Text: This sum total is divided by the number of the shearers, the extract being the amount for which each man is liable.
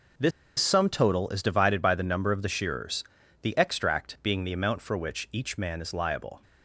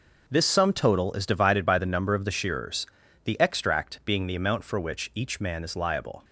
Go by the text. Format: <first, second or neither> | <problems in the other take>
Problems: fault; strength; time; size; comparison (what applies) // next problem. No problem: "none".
second | pauses between "This" and "sum"; slight; at 0.3 s; 0.28 s long